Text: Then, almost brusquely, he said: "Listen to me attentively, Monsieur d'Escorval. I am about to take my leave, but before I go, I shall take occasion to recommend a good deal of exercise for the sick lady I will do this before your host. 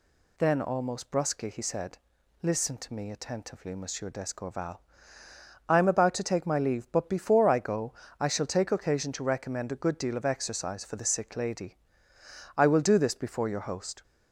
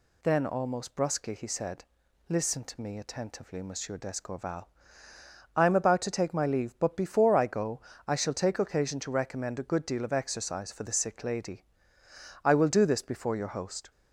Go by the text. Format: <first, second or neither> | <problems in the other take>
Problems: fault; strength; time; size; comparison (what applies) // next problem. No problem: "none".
neither | pauses between "lady" and "I"; noticeable; the same in both